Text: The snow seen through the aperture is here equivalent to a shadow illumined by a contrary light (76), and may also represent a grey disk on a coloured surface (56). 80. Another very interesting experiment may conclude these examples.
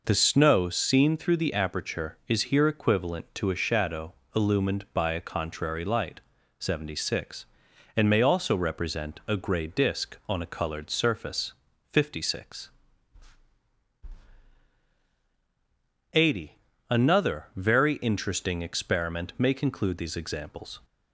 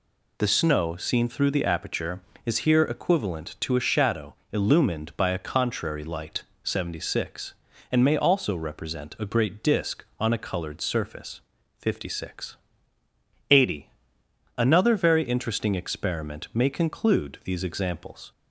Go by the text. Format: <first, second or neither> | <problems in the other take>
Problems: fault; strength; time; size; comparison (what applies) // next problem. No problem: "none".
first | pauses between "shadow" and "illumined"; slight; at 4.3 s; 0.16 s long; slight in the first // says "great" for "grey"; at 9.2 s